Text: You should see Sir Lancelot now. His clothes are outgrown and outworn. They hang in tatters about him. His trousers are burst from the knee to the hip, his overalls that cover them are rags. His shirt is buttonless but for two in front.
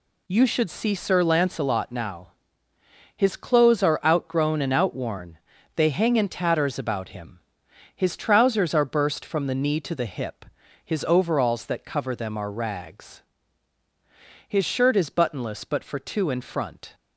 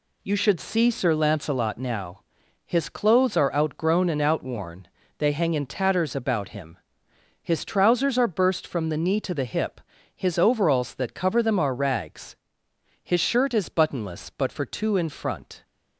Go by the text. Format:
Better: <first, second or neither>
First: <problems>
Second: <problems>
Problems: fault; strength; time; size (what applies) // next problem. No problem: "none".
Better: neither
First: none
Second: none